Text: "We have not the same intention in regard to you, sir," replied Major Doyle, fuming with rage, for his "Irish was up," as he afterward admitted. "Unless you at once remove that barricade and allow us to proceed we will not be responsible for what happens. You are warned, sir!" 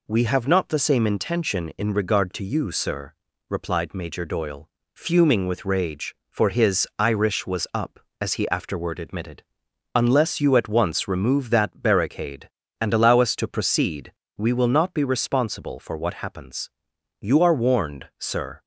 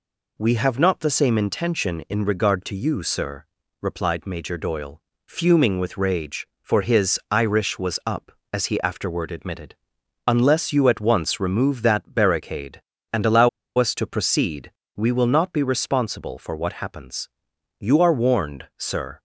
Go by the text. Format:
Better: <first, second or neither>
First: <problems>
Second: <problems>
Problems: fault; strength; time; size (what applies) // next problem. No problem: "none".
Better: first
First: pauses between "proceed" and "we"; slight; at 14.1 s; 0.24 s long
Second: pauses between "allow" and "us"; slight; at 13.4 s; 0.28 s long // pauses between "proceed" and "we"; slight; at 14.7 s; 0.24 s long